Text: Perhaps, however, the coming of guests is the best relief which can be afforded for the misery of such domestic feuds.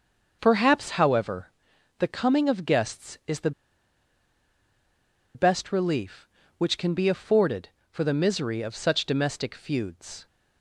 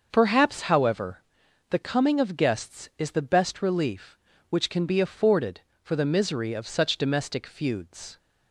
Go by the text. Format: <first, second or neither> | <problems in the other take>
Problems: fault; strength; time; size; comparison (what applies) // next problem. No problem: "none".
second | starts louder than the rest; until 1.4 s; 6.5 dB; also in the second // pauses between "the" and "best"; strong; at 3.5 s; 1.8 s long